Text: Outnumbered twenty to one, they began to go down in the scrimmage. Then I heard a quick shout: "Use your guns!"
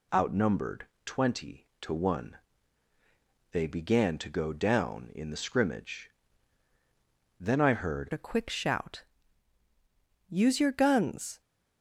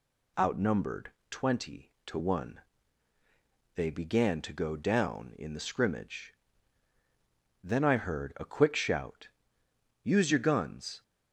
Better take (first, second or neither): second